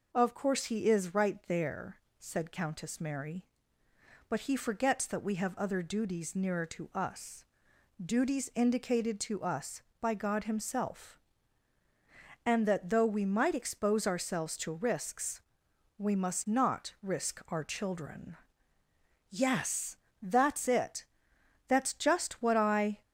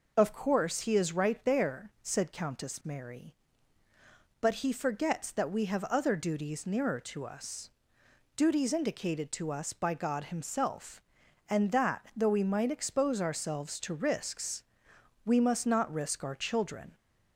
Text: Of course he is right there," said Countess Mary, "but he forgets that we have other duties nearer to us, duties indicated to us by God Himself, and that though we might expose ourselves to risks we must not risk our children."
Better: second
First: pauses between "risks" and "we"; noticeable; at 15.3 s; 0.58 s long // goes on to say "Yes that's it That's just what I"; strong; from 19.3 s on; 3.7 s long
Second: pauses between "risks" and "we"; noticeable; at 14.6 s; 0.62 s long

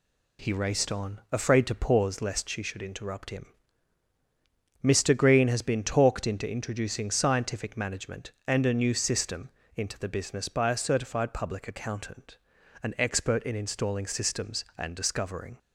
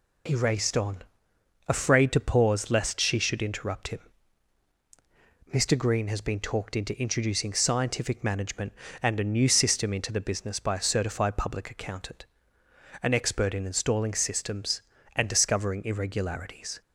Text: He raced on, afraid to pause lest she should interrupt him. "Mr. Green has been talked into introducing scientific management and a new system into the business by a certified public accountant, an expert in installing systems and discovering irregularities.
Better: second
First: pauses between "system" and "into"; slight; at 9.5 s; 0.26 s long // stops before "irregularities"; at 15.5 s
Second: none

